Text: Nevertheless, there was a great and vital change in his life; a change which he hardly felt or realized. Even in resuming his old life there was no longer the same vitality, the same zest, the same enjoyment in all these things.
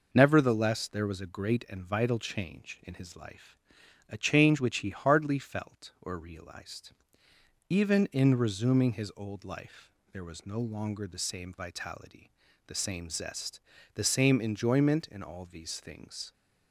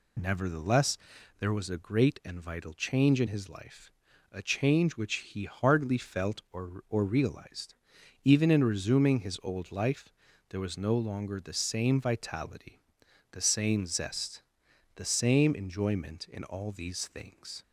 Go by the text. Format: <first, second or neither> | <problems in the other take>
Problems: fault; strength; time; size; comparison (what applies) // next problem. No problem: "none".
first | says "or" twice; at 6.8 s // pauses between "life" and "there"; at 10.1 s; 0.38 s long; slight in the first